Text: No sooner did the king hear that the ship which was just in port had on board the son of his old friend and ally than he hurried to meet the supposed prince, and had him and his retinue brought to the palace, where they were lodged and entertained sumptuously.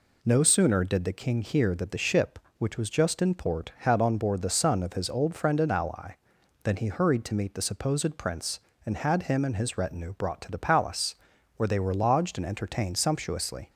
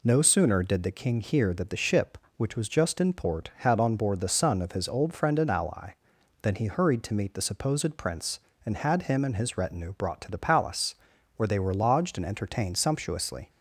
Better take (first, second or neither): neither